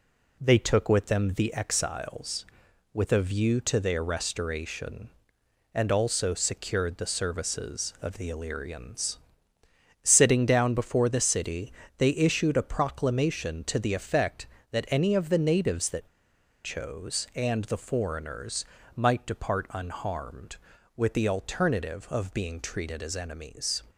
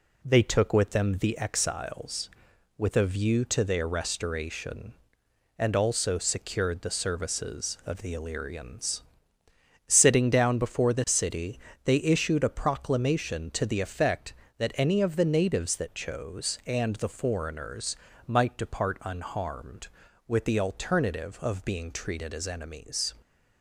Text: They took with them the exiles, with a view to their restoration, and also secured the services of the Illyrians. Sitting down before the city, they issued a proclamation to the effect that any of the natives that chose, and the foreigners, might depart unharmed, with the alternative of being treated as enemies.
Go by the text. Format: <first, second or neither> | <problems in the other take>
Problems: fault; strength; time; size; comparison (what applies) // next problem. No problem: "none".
second | pauses between "that" and "chose"; noticeable; at 16.0 s; 0.56 s long